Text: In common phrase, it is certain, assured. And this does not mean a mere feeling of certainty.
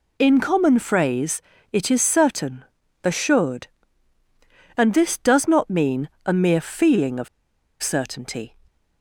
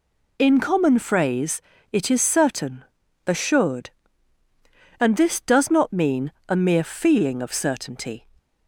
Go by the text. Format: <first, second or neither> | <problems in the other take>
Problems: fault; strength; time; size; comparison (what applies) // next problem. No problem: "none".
second | pauses between "mean" and "a"; slight; at 6.0 s; 0.16 s long; slight in the second // pauses between "of" and "certainty"; noticeable; at 7.2 s; 0.54 s long